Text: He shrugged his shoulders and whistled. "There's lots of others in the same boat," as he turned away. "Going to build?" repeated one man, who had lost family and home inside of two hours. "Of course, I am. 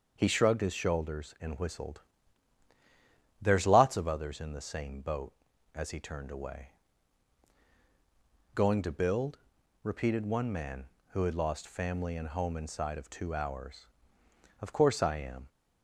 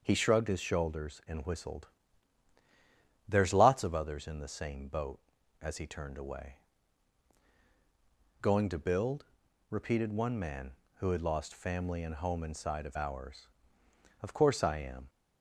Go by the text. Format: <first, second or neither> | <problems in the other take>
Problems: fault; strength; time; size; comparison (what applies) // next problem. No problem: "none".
first | skips "two"; at 12.9 s